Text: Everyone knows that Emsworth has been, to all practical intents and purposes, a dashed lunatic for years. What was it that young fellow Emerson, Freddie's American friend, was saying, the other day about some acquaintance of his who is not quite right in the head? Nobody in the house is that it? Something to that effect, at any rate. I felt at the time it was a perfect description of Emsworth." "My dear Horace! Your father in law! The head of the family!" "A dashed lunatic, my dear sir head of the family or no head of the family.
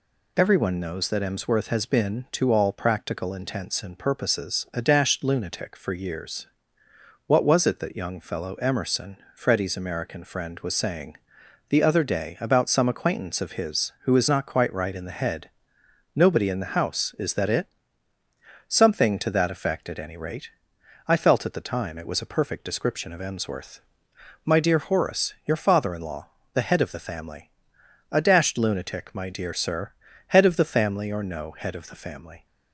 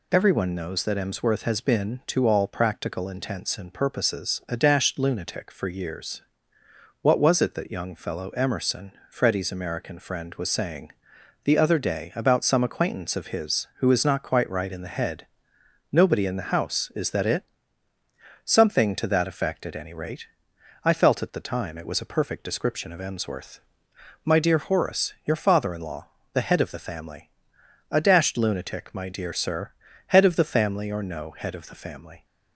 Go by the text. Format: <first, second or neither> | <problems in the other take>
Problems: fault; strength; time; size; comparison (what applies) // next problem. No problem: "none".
neither | pauses between "sir" and "head"; the same in both